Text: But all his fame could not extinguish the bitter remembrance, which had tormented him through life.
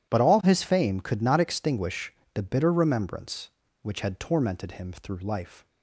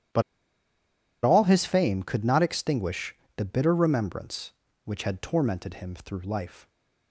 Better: first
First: starts louder than the rest; strong; until 1.1 s; 11 dB // pauses between "extinguish" and "the"; slight; at 2.1 s; 0.20 s long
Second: starts louder than the rest; strong; until 2.1 s; 10.5 dB // pauses between "But" and "all"; at 0.2 s; 1.0 s long // pauses between "extinguish" and "the"; slight; at 3.1 s; 0.20 s long

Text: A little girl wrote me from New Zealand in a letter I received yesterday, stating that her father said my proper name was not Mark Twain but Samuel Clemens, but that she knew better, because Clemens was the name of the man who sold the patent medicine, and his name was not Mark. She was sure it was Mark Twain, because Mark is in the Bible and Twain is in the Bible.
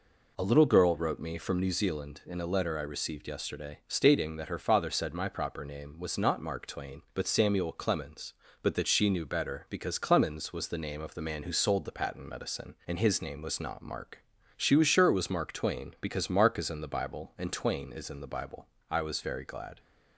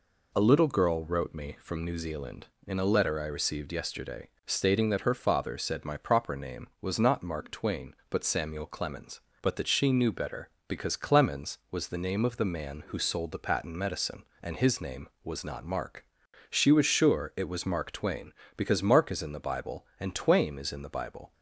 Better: second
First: goes on to say "I was very glad"; noticeable; from 18.8 s on; 0.90 s long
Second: none

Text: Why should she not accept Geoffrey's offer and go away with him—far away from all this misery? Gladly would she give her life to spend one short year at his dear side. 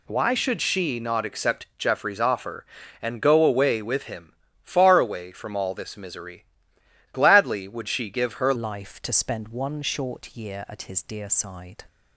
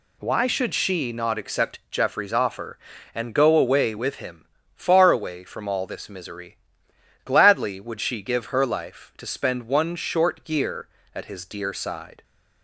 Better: second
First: changes voice at "life"; from 8.5 s on; 3.3 s long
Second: none

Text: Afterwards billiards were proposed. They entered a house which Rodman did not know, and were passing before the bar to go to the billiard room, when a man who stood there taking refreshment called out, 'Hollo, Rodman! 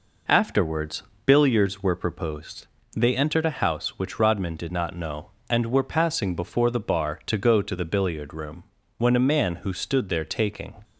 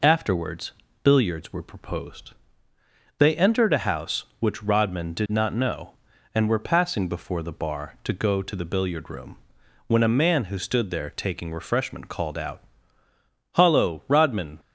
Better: second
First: pauses between "Afterwards" and "billiards"; slight; at 1.0 s; 0.24 s long // stops before "refreshment called out Hollo Rodman"; at 10.8 s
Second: pauses between "Afterwards" and "billiards"; slight; at 0.7 s; 0.32 s long

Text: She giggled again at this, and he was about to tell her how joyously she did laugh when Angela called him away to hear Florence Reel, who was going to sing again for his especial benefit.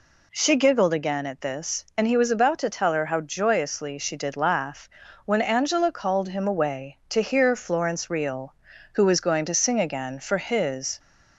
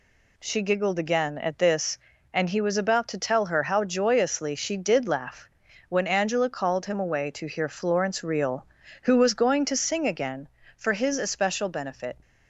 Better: second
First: pauses between "laugh" and "when"; at 4.8 s; 0.38 s long // stops before "especial benefit"; at 10.9 s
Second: pauses between "laugh" and "when"; at 5.4 s; 0.40 s long

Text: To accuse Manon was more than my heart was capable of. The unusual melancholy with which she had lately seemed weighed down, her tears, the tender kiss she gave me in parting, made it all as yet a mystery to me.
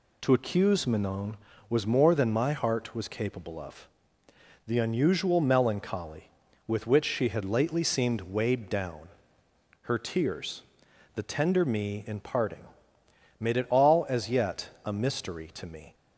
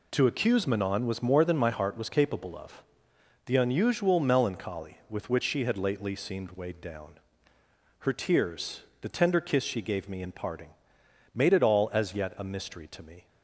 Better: second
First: skips "kiss she gave"; at 11.6 s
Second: none

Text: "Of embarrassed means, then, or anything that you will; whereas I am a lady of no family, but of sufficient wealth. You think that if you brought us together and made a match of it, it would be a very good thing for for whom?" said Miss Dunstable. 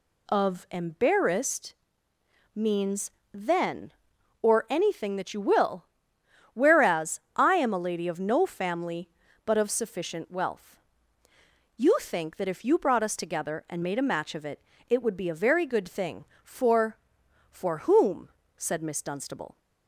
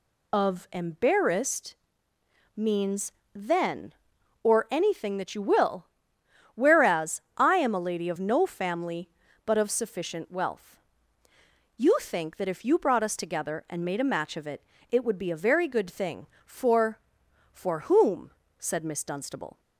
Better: first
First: pauses between "embarrassed" and "means"; noticeable; at 1.7 s; 0.80 s long // pauses between "whereas" and "I"; slight; at 7.1 s; 0.16 s long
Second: loses the start of "Of"; at 0.3 s; 45 ms // pauses between "embarrassed" and "means"; noticeable; at 1.7 s; 0.80 s long // pauses between "whereas" and "I"; slight; at 7.2 s; 0.16 s long

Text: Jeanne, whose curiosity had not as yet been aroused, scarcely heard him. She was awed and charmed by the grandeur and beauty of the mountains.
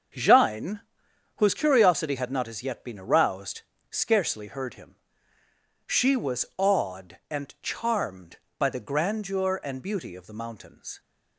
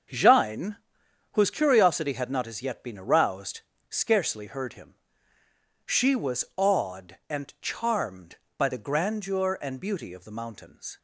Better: neither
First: starts louder than the rest; until 1.7 s; 7 dB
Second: starts louder than the rest; until 1.6 s; 7 dB

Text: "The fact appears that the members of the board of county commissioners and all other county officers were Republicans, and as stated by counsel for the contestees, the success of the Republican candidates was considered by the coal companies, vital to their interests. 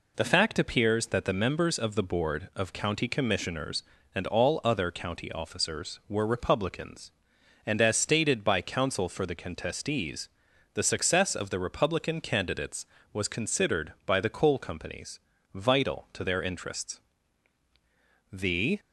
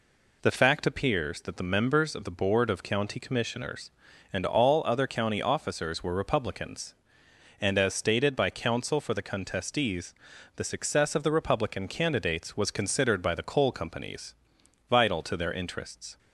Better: second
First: goes on to say "The"; slight; from 18.3 s on; 0.48 s long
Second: none

